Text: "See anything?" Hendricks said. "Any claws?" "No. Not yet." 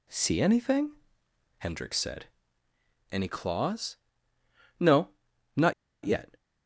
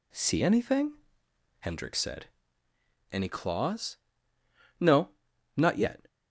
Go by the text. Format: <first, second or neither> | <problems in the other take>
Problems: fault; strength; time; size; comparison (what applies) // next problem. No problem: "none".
second | pauses between "Not" and "yet"; slight; at 5.7 s; 0.32 s long